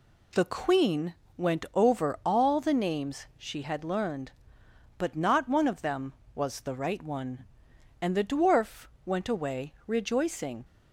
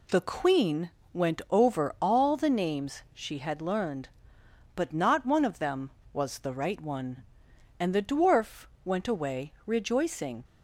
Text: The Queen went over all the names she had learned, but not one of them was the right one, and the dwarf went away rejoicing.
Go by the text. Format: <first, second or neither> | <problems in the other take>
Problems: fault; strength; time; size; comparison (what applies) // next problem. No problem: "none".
neither | pauses between "Queen" and "went"; slight; the same in both // pauses between "dwarf" and "went"; slight; the same in both